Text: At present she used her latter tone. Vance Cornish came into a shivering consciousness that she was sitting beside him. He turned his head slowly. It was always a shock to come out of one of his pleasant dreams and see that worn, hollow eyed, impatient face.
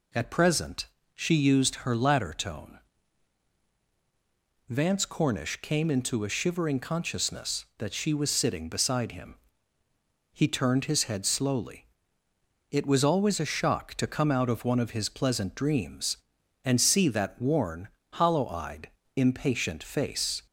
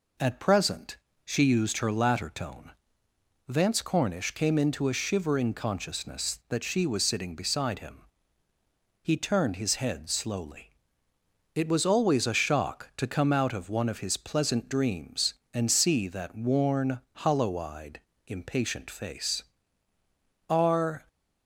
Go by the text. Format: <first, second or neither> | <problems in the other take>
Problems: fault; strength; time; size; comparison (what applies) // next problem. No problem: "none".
first | pauses between "present" and "she"; slight; at 0.9 s; 0.28 s long; slight in the first // goes on to say "Are"; from 20.4 s on; 0.58 s long